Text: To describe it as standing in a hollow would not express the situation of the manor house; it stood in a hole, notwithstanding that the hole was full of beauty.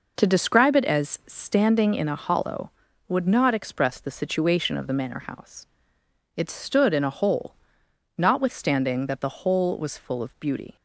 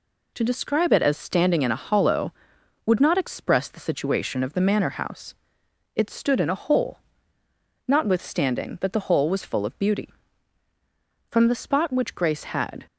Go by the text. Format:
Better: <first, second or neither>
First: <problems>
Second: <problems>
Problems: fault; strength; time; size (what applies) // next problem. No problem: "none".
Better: first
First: none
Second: goes on to say "From the spot which Grace had"; from 11.2 s on; 1.5 s long